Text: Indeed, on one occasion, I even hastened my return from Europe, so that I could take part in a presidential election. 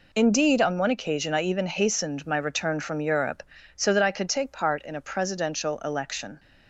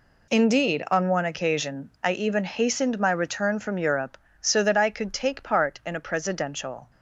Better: first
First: none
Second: stops before "election"; at 6.8 s

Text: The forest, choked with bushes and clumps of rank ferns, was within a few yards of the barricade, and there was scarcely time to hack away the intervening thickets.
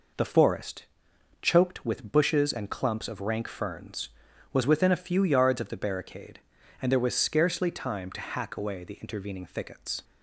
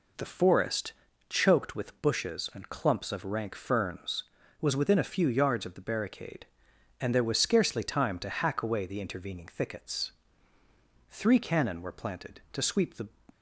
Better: first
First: none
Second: goes on to say "Three cannon were planted to sweep the"; strong; from 11.1 s on; 1.9 s long

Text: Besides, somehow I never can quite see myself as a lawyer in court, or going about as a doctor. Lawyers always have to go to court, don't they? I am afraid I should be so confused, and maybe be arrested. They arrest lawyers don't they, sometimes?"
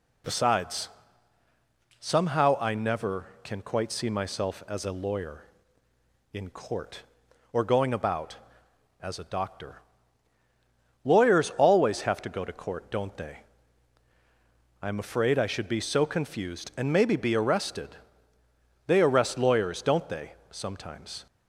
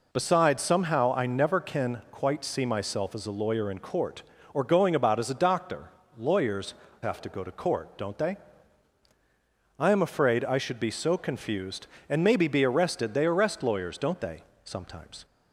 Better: first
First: none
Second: skips "always"; at 6.8 s

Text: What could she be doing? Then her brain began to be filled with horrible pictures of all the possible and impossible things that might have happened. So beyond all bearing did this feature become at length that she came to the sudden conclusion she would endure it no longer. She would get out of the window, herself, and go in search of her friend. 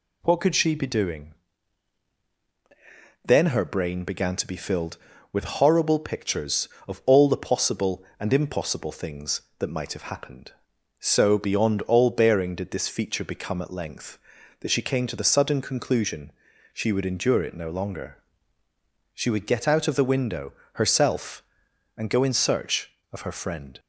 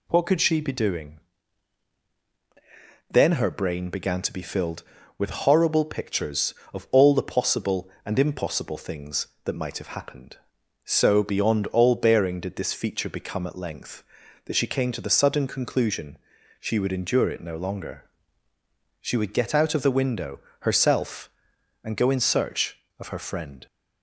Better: neither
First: pauses between "conclusion" and "she"; at 16.3 s; 0.41 s long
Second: pauses between "conclusion" and "she"; at 16.1 s; 0.42 s long

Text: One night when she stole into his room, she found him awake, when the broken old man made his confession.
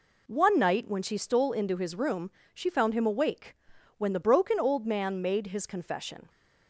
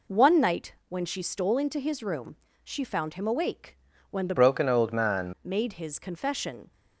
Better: first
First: none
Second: pauses between "night" and "when"; slight; at 0.7 s; 0.16 s long // changes voice from "broken" to "man"; from 4.3 to 5.3 s; 1.0 s long

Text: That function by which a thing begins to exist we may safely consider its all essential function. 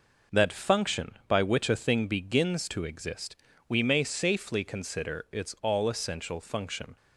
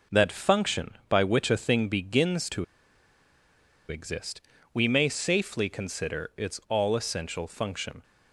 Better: first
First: pauses between "exist" and "we"; slight; at 3.3 s; 0.32 s long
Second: pauses between "to" and "exist"; at 2.6 s; 1.2 s long // pauses between "exist" and "we"; slight; at 4.4 s; 0.32 s long

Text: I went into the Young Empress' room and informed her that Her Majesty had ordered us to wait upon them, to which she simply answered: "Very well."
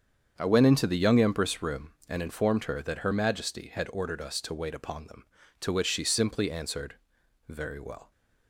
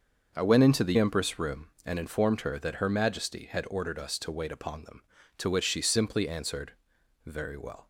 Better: first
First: starts louder than the rest; strong; until 1.3 s; 7.5 dB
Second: starts louder than the rest; until 1.3 s; 6.5 dB // skips "Young"; at 0.9 s

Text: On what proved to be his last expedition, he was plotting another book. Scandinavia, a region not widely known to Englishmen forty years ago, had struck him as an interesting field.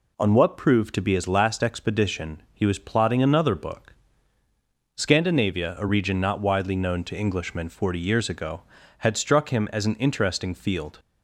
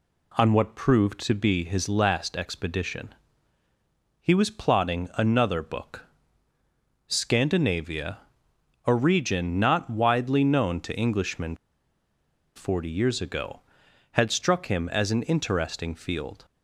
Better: first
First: none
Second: pauses between "Englishmen" and "forty"; at 11.5 s; 0.99 s long

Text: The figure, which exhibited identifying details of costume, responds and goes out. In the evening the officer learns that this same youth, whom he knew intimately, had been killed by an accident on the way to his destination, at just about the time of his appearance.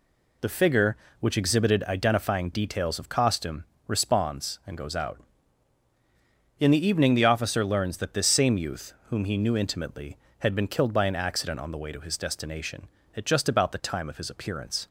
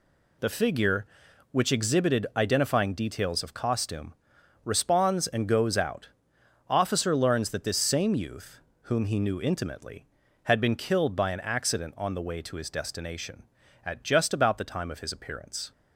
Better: first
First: none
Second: skips "In the evening the"; at 6.3 s

